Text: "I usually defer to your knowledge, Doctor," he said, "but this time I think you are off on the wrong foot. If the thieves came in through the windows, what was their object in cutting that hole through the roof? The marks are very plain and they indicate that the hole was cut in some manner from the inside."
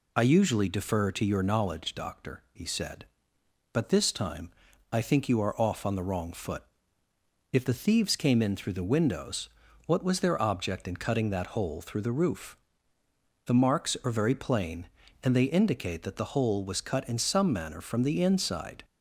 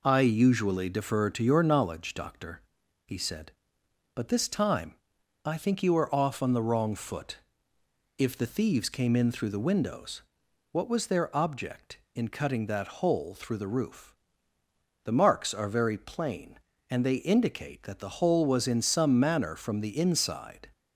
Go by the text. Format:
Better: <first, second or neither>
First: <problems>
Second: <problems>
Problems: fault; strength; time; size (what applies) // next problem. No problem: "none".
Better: first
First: pauses between "time" and "I"; at 4.5 s; 0.40 s long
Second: pauses between "time" and "I"; noticeable; at 4.9 s; 0.48 s long // skips "cut"; at 18.6 s